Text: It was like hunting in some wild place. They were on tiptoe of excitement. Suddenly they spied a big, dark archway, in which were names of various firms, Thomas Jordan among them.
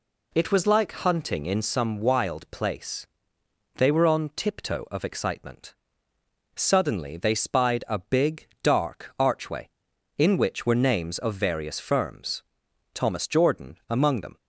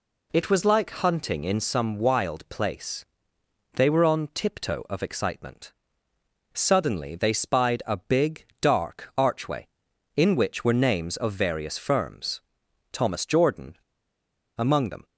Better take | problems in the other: first | pauses between "Jordan" and "among"; noticeable; at 13.7 s; 0.80 s long

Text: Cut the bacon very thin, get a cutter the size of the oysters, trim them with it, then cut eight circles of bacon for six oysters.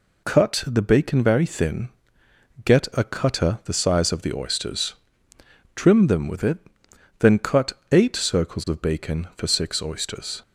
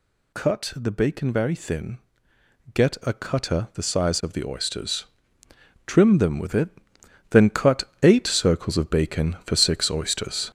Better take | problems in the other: first | gets louder; noticeable; throughout; 6 dB // pauses between "cut" and "eight"; slight; at 7.8 s; 0.18 s long; slight in the first

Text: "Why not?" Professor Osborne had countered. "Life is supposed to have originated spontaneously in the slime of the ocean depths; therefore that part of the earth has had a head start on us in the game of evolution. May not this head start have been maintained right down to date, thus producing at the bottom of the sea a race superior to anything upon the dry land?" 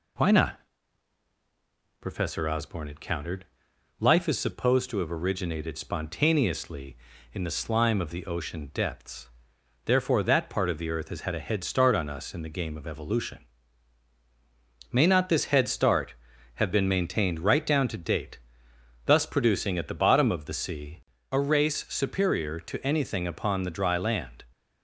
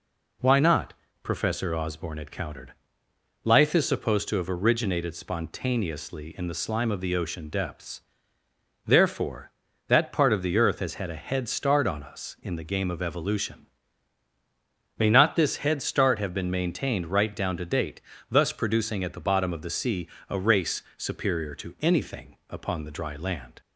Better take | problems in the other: neither | pauses between "sea" and "a"; slight; the same in both

